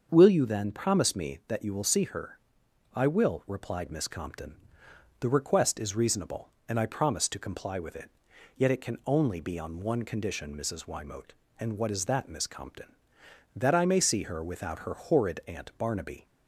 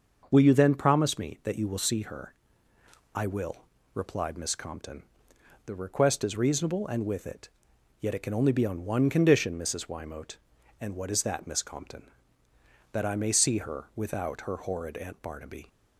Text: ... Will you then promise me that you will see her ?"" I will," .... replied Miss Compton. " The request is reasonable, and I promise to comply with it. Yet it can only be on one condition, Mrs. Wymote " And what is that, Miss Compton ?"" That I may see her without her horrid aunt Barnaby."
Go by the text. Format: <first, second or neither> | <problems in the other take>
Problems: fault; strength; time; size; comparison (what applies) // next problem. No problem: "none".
first | starts louder than the rest; noticeable; until 1.2 s; 6 dB; also in the first // skips "I promise to comply"; at 7.0 s